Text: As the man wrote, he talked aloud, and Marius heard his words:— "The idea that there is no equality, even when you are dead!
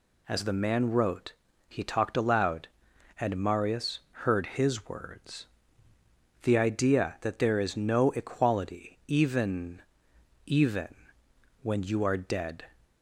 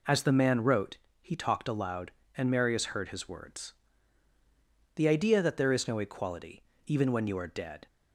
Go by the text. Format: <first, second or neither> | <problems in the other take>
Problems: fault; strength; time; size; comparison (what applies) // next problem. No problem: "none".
second | pauses between "Marius" and "heard"; slight; at 3.9 s; 0.22 s long // says "even" twice; at 10.4 s